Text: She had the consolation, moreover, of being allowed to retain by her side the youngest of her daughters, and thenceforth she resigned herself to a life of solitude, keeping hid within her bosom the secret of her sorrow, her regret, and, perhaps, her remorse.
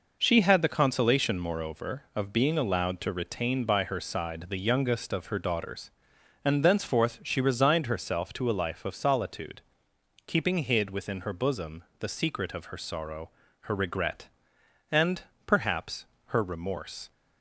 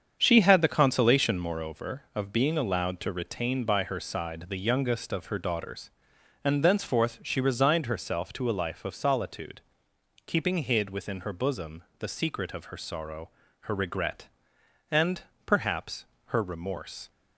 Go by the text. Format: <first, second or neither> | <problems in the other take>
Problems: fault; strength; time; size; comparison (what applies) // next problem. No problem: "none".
first | starts louder than the rest; strong; until 1.6 s; 7.5 dB // pauses between "bosom" and "the"; slight; at 11.8 s; 0.16 s long; slight in the first